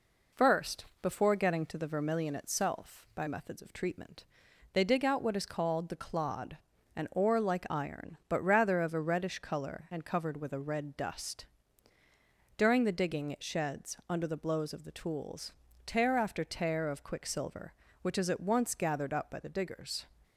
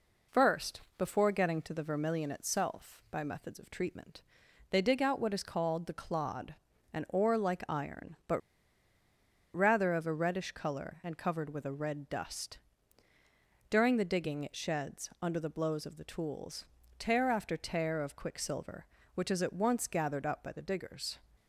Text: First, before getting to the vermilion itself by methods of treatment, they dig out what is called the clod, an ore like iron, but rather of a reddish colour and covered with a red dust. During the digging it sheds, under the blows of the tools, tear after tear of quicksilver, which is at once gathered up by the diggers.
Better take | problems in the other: first | pauses between "but" and "rather"; at 8.4 s; 1.1 s long

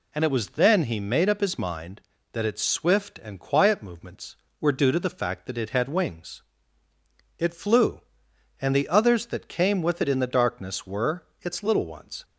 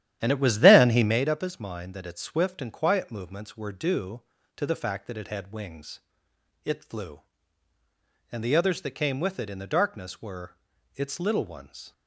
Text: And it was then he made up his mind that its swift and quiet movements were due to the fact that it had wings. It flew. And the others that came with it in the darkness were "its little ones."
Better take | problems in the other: first | starts louder than the rest; strong; until 1.2 s; 11.5 dB // pauses between "were" and "its"; at 10.5 s; 0.38 s long; slight in the first

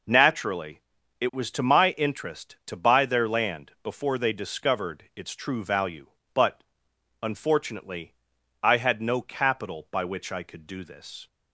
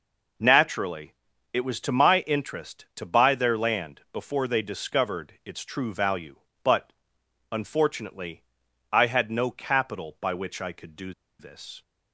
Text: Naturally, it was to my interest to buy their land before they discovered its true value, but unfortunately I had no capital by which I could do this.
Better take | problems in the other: first | pauses between "but" and "unfortunately"; noticeable; at 6.9 s; 0.60 s long; noticeable in the first // pauses between "unfortunately" and "I"; noticeable; at 8.4 s; 0.48 s long; noticeable in the first // pauses between "do" and "this"; slight; at 11.1 s; 0.27 s long

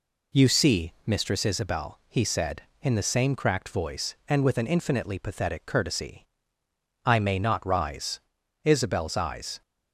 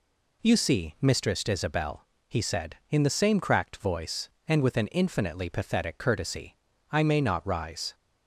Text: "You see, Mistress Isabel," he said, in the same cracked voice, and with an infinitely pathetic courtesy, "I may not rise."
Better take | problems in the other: second | goes on to say "Isabel's eyes"; noticeable; from 8.6 s on; 0.98 s long

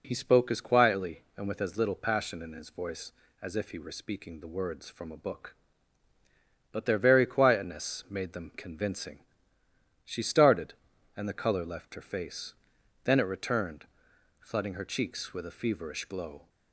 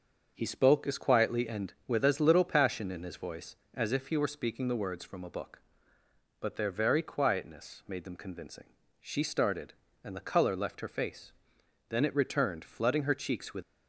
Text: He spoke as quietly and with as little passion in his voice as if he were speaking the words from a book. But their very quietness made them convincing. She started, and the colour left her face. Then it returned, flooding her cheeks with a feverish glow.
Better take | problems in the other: first | starts louder than the rest; until 1.3 s; 6.5 dB // stops before "a feverish glow"; at 13.6 s

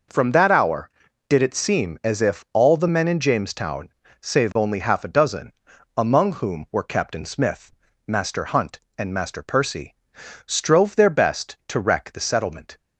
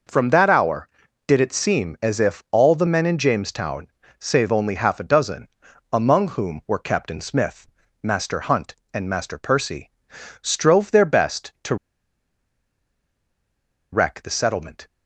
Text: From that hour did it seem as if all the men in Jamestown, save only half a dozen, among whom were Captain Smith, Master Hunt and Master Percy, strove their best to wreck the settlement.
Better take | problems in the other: first | pauses between "to" and "wreck"; strong; at 11.7 s; 2.1 s long

